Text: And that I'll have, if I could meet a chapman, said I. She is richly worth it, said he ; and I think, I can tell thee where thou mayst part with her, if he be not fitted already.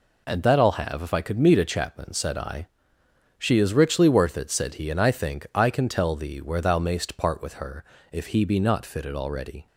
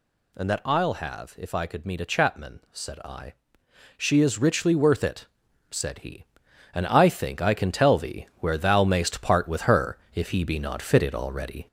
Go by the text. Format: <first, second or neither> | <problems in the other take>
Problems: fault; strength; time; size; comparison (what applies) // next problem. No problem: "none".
first | gets louder; noticeable; throughout; 4 dB